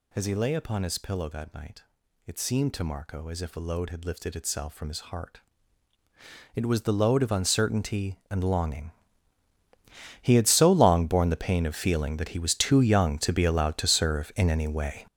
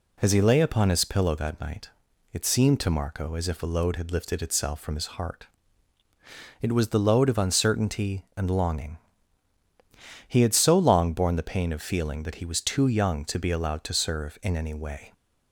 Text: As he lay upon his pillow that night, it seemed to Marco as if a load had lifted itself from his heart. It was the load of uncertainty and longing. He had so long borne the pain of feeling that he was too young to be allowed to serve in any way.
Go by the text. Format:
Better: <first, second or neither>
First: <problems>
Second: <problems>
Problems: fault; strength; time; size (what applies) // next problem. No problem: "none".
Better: second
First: gets louder; strong; throughout; 10.5 dB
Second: none